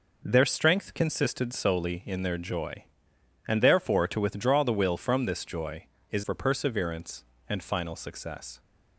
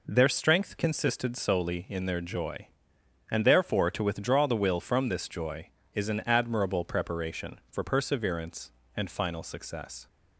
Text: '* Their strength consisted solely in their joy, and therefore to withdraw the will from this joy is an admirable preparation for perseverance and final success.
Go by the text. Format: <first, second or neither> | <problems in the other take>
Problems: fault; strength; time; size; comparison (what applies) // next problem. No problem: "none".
second | skips "an admirable preparation"; at 6.2 s